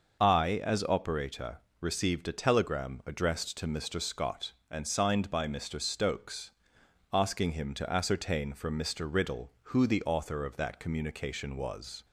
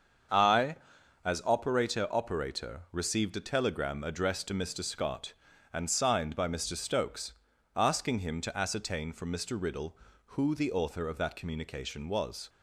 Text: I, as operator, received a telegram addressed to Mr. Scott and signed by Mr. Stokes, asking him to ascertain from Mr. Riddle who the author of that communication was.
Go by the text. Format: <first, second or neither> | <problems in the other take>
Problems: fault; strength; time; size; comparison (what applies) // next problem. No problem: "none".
first | starts louder than the rest; until 1.7 s; 7 dB // says "operator" twice; at 2.0 s